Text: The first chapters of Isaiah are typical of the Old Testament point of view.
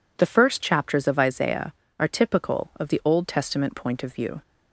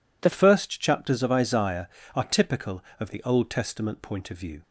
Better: first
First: none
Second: changes voice at "first"; from 0.3 s on; 4.3 s long

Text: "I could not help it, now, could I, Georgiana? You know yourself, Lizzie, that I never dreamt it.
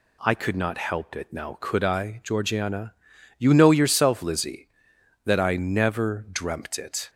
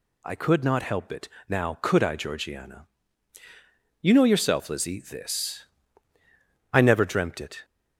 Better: first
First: none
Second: says "this" for "that"; at 5.0 s

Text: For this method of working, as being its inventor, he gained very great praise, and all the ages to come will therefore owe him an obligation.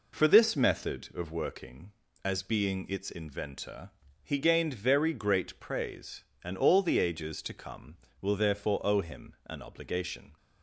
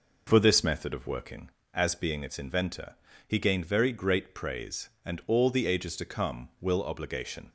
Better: first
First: none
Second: skips "therefore owe him an"; at 6.8 s

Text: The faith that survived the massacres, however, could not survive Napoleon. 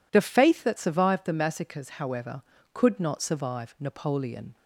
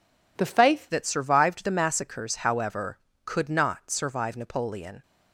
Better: first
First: none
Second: changes voice at "that"; from 0.8 s on; 4.2 s long

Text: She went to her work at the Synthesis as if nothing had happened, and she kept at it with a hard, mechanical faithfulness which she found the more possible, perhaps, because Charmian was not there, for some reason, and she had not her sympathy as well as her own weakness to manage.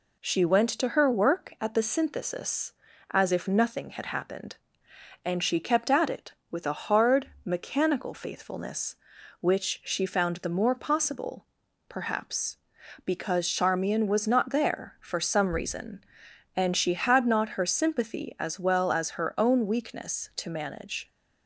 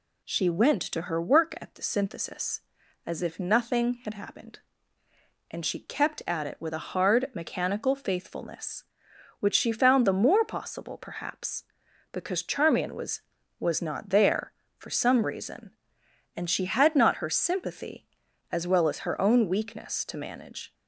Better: first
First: none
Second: says "was" twice; at 13.5 s

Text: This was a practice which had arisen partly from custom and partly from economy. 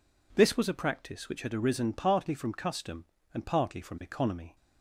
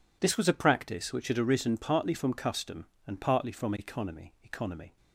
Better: first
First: none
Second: says "economy" twice; at 4.4 s

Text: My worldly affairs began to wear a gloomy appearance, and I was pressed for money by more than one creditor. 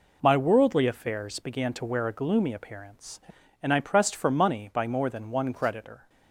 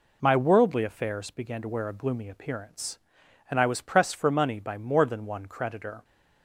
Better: second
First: skips "was"; at 3.7 s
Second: none

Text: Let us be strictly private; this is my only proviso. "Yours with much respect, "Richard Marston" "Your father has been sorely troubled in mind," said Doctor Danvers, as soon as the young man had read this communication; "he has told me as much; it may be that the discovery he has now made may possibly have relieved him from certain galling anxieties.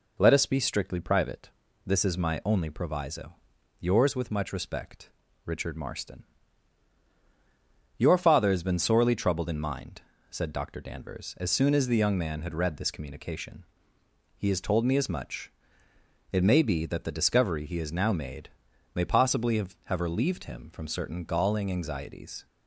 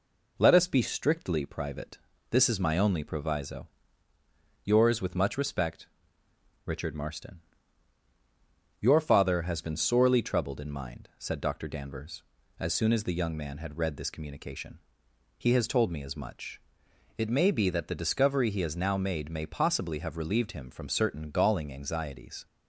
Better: second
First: pauses between "Marston" and "Your"; strong; at 6.2 s; 1.7 s long // pauses between "made" and "may"; at 18.4 s; 0.44 s long // says "have" twice; at 19.8 s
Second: pauses between "Marston" and "Your"; strong; at 7.4 s; 1.3 s long

